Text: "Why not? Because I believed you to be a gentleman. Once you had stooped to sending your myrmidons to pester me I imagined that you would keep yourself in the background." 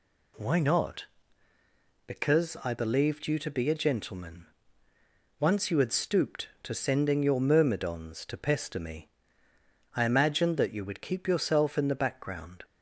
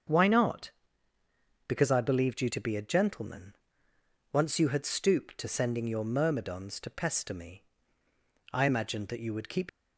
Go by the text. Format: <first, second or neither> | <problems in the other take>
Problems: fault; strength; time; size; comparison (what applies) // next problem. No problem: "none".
first | starts louder than the rest; until 2.0 s; 7 dB // pauses between "me" and "I"; noticeable; at 7.6 s; 0.88 s long; noticeable in the first // stops before "yourself in the background"; at 9.6 s